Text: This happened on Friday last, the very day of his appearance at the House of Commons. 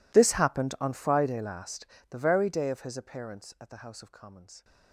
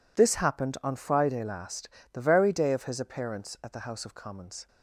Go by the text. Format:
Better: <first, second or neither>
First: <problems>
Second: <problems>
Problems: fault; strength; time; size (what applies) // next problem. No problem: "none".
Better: second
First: gets quieter; strong; throughout; 27 dB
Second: none